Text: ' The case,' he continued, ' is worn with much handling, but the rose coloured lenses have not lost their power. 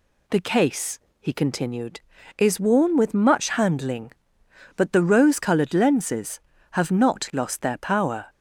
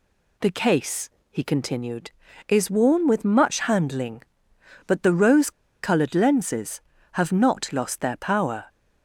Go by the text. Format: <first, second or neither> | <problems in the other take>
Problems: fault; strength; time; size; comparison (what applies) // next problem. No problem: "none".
first | pauses between "rose" and "coloured"; slight; at 5.4 s; 0.33 s long